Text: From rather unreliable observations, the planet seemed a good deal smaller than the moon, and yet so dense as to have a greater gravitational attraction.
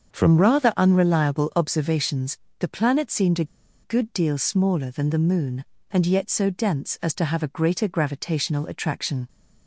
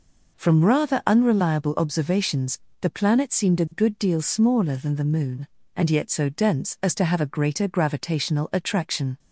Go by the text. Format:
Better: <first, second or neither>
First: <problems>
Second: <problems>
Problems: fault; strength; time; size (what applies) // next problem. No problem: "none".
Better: second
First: starts louder than the rest; until 1.1 s; 7 dB // pauses between "a" and "good"; at 3.4 s; 0.37 s long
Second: none